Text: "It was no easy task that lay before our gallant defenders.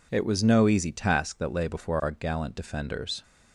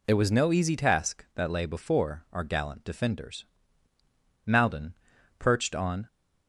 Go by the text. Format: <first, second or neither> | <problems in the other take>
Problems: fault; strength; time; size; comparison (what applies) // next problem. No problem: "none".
first | goes on to say "Maldon perched on"; from 4.4 s on; 1.6 s long